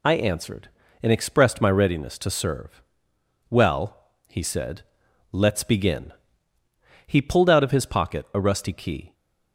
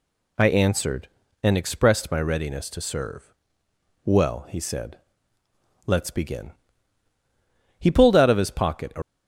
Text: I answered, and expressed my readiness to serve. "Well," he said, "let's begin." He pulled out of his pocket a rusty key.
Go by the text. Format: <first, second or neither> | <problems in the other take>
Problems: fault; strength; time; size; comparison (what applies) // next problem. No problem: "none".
first | stops before "rusty key"; at 9.0 s